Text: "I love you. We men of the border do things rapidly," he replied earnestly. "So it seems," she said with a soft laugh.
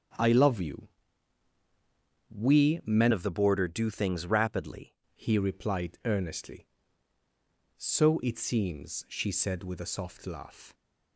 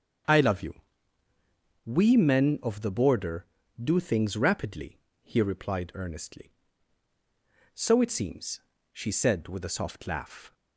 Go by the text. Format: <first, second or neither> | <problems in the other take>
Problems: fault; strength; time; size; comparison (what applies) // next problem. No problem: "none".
second | starts louder than the rest; strong; until 2.6 s; 7 dB; strong in the second // changes voice from "of" to "rapidly"; from 3.1 to 4.9 s; 1.8 s long